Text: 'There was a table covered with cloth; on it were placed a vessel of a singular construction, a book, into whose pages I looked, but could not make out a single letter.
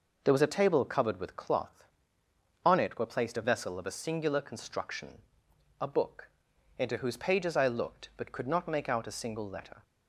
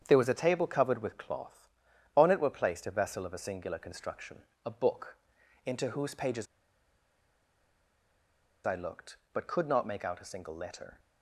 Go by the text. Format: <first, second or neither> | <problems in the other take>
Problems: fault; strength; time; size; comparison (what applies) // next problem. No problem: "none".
first | starts louder than the rest; strong; until 1.0 s; 8 dB // pauses between "pages" and "I"; strong; at 6.4 s; 2.2 s long